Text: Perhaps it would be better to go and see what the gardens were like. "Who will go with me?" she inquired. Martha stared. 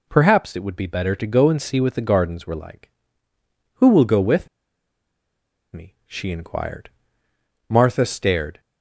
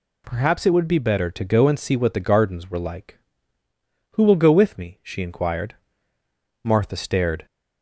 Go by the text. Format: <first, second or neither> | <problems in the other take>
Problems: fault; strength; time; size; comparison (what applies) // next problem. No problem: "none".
second | pauses between "with" and "me"; strong; at 4.4 s; 1.2 s long